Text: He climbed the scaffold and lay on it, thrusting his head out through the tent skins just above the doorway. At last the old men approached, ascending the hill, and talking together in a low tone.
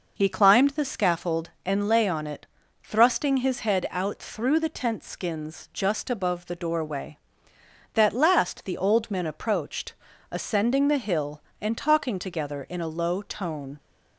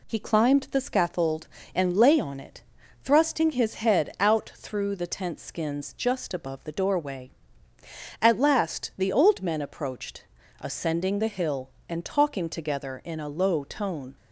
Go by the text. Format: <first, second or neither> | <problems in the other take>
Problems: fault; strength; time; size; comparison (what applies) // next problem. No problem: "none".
second | says "That" for "At"; at 7.9 s